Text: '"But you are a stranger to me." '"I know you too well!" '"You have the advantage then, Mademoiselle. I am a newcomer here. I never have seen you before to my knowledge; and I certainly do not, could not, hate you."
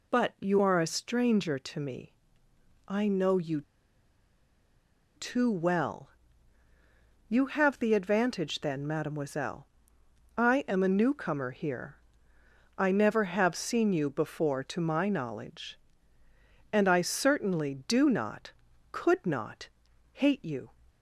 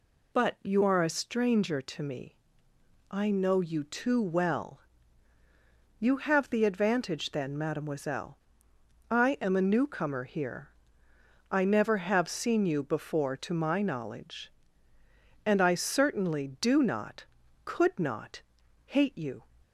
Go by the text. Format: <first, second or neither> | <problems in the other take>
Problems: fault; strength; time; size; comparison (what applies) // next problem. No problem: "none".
second | pauses between "you" and "too"; strong; at 3.6 s; 1.5 s long